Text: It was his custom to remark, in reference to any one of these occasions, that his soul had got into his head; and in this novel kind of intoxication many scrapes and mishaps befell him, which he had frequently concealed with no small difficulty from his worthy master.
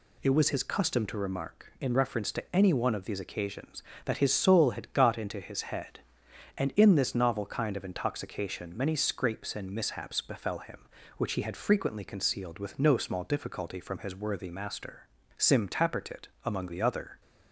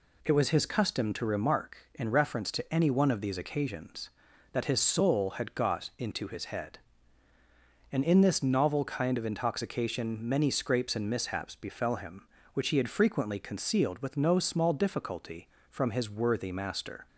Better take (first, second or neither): second